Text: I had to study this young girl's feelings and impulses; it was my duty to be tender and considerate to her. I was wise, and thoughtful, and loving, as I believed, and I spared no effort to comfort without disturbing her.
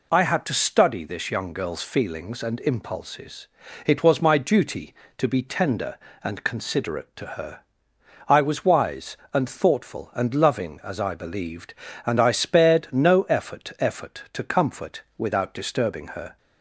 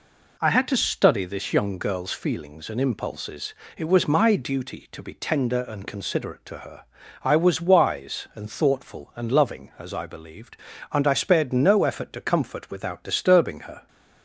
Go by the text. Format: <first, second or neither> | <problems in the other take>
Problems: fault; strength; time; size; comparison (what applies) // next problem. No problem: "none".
second | says "effort" twice; at 13.8 s // pauses between "comfort" and "without"; slight; at 15.0 s; 0.16 s long